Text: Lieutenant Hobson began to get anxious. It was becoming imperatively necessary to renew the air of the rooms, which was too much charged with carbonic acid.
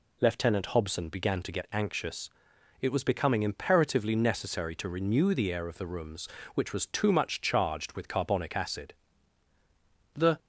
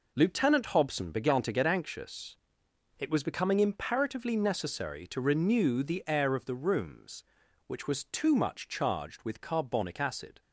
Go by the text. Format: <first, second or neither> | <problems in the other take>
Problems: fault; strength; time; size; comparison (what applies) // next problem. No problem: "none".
second | goes on to say "The"; slight; from 10.1 s on; 0.24 s long